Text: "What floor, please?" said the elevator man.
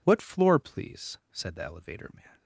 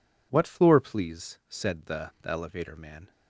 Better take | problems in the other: first | says "the" twice; at 2.2 s

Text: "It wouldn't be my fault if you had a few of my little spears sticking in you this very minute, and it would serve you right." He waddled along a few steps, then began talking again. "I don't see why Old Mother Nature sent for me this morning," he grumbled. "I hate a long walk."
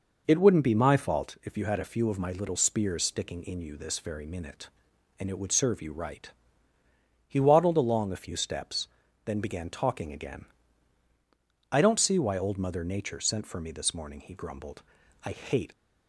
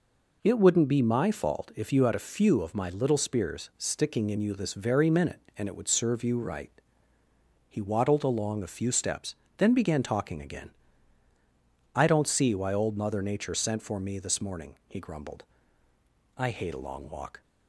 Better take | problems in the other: second | stops before "a long walk"; at 15.7 s

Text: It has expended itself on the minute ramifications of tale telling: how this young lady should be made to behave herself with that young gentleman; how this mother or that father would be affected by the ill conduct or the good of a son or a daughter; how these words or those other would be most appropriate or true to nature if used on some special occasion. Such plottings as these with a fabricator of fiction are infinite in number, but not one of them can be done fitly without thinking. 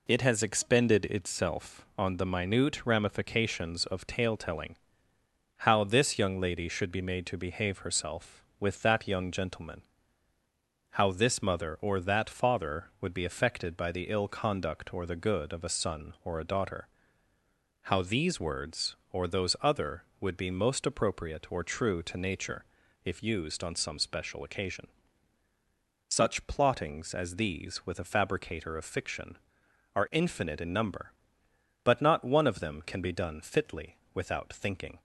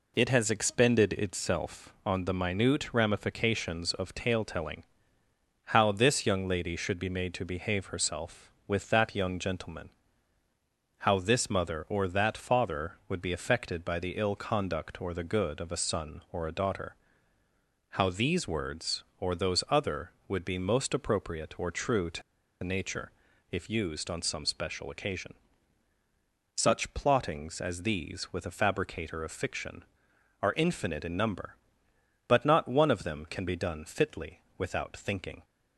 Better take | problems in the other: first | pauses between "to" and "nature"; at 22.2 s; 0.40 s long // pauses between "nature" and "if"; at 23.0 s; 0.40 s long; also in the first // pauses between "fitly" and "without"; slight; at 34.4 s; 0.16 s long; slight in the first

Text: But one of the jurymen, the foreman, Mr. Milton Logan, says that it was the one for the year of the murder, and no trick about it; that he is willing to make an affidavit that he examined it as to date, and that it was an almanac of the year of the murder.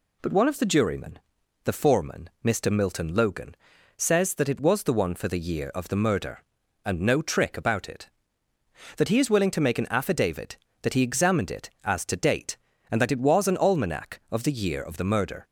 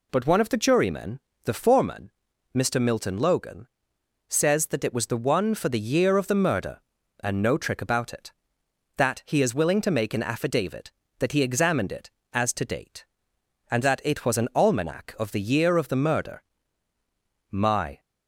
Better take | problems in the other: first | goes on to say "My"; slight; from 17.5 s on; 0.48 s long

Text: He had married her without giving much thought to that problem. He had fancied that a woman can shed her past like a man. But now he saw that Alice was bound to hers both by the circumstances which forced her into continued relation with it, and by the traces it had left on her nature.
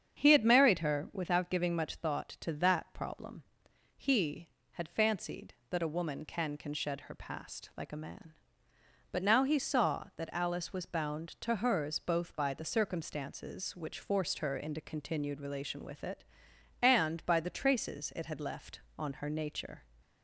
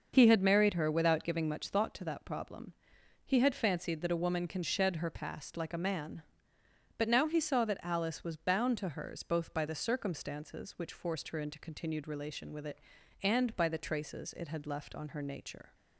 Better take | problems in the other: second | starts louder than the rest; strong; until 1.2 s; 7.5 dB; also in the second // says "can" twice; at 6.5 s

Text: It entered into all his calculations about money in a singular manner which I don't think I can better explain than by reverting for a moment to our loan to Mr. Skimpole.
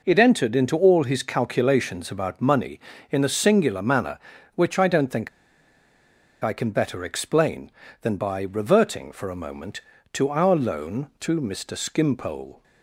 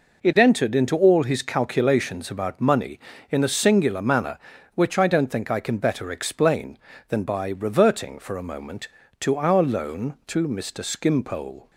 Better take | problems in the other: second | pauses between "think" and "I"; at 5.2 s; 1.1 s long

